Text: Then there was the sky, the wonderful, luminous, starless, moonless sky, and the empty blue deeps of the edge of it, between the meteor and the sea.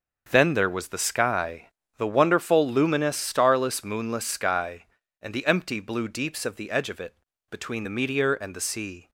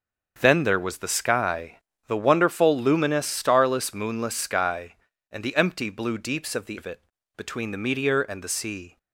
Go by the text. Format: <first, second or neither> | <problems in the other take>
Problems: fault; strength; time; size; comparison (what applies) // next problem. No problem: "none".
first | starts louder than the rest; until 1.4 s; 6.5 dB; also in the first // skips "edge"; at 6.7 s